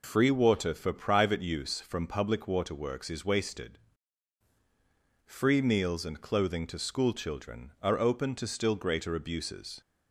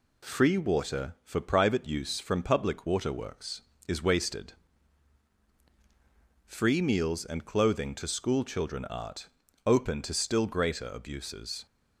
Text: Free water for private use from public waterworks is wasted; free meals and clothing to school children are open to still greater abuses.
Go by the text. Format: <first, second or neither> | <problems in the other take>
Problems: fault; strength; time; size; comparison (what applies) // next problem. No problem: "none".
first | says "art" for "are"; at 8.8 s